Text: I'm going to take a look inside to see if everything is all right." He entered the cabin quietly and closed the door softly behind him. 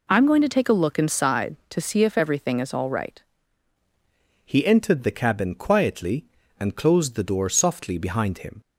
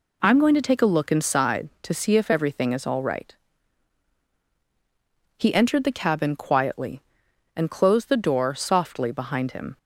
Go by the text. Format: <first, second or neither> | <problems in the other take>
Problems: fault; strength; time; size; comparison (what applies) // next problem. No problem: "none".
second | changes voice at "He"; from 4.4 s on; 4.1 s long